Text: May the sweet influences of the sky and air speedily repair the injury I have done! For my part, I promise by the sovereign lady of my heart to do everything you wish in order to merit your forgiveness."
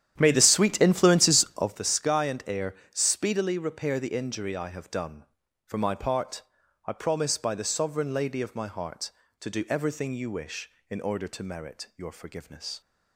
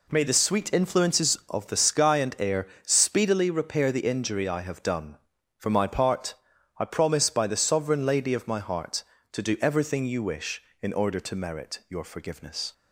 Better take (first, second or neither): second